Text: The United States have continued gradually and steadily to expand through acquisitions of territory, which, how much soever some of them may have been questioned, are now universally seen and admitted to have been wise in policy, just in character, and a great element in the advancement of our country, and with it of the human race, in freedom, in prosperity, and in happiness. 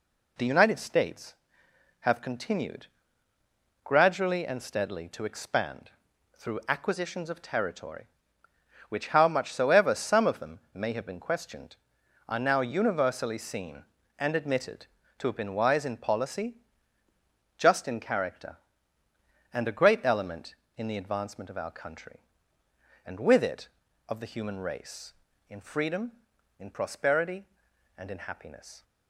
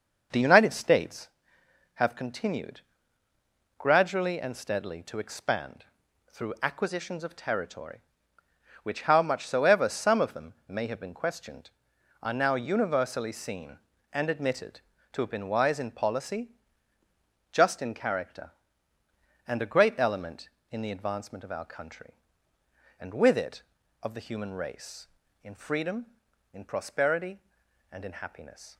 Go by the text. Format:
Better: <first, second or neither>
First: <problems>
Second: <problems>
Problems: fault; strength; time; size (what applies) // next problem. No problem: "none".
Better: first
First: pauses between "continued" and "gradually"; noticeable; at 2.8 s; 0.98 s long // pauses between "expand" and "through"; noticeable; at 5.8 s; 0.48 s long // pauses between "them" and "may"; slight; at 10.5 s; 0.16 s long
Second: starts louder than the rest; noticeable; until 1.4 s; 6 dB // pauses between "continued" and "gradually"; noticeable; at 2.7 s; 0.98 s long // pauses between "expand" and "through"; noticeable; at 5.8 s; 0.48 s long // pauses between "them" and "may"; slight; at 10.5 s; 0.16 s long